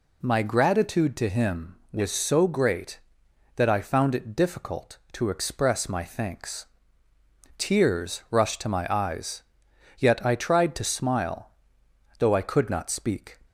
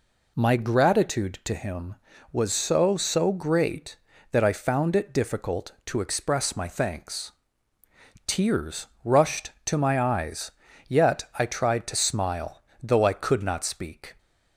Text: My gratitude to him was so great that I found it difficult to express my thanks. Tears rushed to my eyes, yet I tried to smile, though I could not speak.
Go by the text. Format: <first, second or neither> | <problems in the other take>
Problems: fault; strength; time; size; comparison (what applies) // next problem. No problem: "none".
first | says "so" twice; at 2.9 s // pauses between "Tears" and "rushed"; slight; at 8.8 s; 0.16 s long